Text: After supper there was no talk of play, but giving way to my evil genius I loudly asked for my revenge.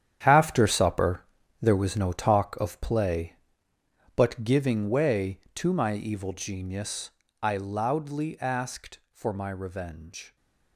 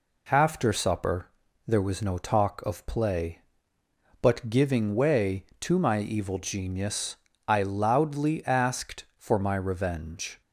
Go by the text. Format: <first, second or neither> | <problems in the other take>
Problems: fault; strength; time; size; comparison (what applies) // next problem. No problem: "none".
second | gets quieter; strong; throughout; 13 dB // pauses between "supper" and "there"; slight; at 1.2 s; 0.36 s long; slight in the second // pauses between "genius" and "I"; slight; at 7.0 s; 0.32 s long; slight in the second